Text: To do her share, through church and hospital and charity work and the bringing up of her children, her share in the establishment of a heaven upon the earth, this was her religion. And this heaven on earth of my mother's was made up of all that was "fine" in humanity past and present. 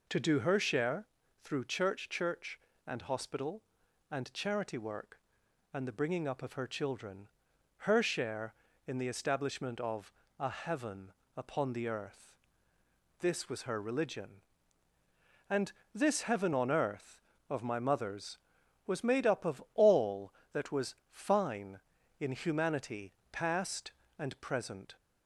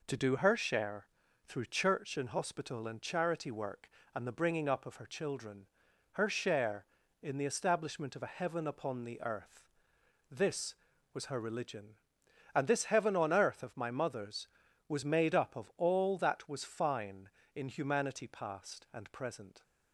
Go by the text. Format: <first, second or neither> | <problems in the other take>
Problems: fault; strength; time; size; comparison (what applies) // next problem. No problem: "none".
second | says "church" twice; at 2.0 s // pauses between "of" and "a"; slight; at 10.1 s; 0.26 s long // pauses between "heaven" and "upon"; slight; at 11.1 s; 0.26 s long // pauses between "And" and "this"; slight; at 15.7 s; 0.20 s long // pauses between "was" and "fine"; slight; at 20.9 s; 0.18 s long // pauses between "humanity" and "past"; slight; at 23.1 s; 0.20 s long